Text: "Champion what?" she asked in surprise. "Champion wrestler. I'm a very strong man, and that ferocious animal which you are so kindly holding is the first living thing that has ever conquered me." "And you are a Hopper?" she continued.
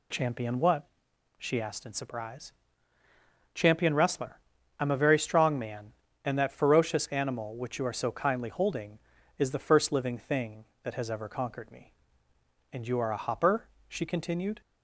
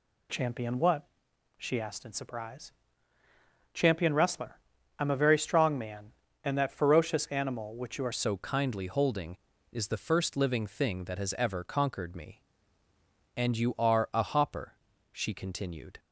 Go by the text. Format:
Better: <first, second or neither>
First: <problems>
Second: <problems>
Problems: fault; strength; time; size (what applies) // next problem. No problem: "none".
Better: first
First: none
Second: changes voice at "so"; from 8.1 s on; 7.8 s long